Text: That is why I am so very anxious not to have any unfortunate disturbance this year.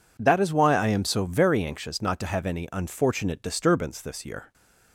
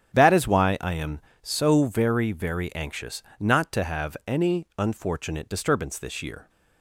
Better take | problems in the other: first | starts louder than the rest; strong; until 1.1 s; 8 dB // says "very" twice; at 2.3 s // pauses between "anxious" and "not"; slight; at 3.2 s; 0.18 s long

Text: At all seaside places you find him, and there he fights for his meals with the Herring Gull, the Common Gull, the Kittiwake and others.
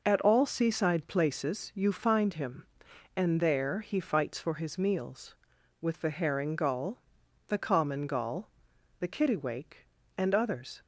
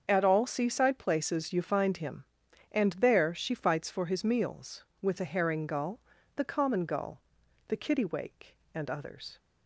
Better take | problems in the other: first | starts louder than the rest; until 1.0 s; 7 dB // says "she" for "he"; at 3.3 s

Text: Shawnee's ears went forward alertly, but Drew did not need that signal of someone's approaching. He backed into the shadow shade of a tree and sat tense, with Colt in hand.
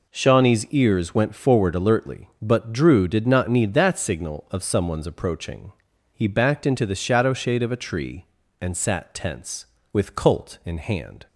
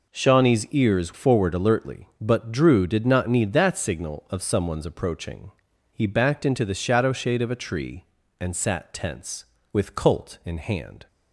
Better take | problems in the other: first | skips "went"; at 1.1 s

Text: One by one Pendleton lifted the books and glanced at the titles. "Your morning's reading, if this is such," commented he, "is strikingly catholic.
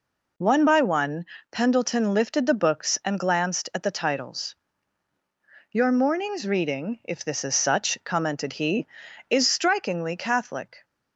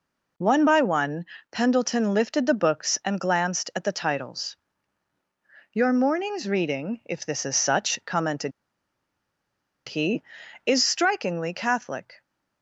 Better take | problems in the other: first | pauses between "one" and "Pendleton"; slight; at 1.2 s; 0.26 s long; slight in the first // pauses between "commented" and "he"; strong; at 8.5 s; 1.3 s long

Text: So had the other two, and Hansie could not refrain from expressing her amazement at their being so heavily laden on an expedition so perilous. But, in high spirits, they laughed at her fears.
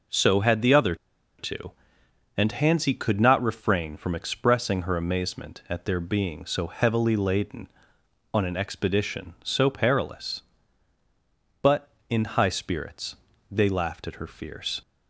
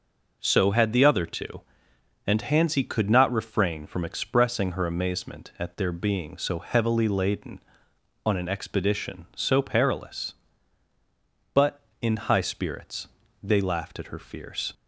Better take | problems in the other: second | pauses between "other" and "two"; at 0.9 s; 0.43 s long

